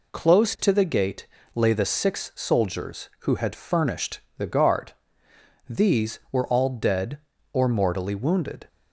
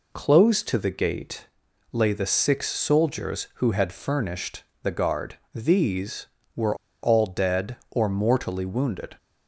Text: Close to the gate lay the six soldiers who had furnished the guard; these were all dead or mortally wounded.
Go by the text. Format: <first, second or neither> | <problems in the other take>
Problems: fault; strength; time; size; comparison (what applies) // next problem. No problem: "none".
first | pauses between "gate" and "lay"; at 1.4 s; 0.44 s long; slight in the first // pauses between "furnished" and "the"; slight; at 4.6 s; 0.22 s long; slight in the first // pauses between "were" and "all"; slight; at 6.7 s; 0.27 s long